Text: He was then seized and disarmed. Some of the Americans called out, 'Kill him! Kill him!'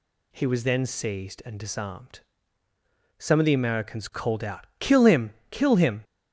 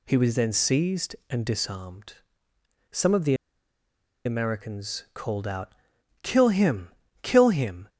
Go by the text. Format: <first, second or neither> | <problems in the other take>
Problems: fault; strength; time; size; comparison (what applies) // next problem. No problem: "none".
first | pauses between "the" and "Americans"; noticeable; at 3.3 s; 0.89 s long